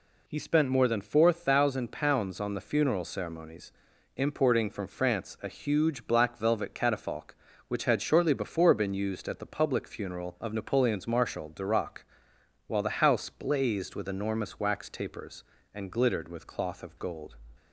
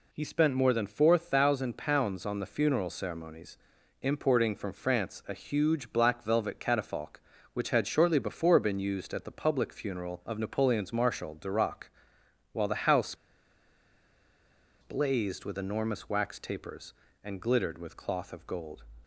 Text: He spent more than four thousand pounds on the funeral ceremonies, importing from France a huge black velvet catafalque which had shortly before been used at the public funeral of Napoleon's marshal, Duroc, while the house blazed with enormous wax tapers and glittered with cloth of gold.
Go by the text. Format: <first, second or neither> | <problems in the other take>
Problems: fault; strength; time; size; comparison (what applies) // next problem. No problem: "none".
first | pauses between "house" and "blazed"; strong; at 13.1 s; 1.6 s long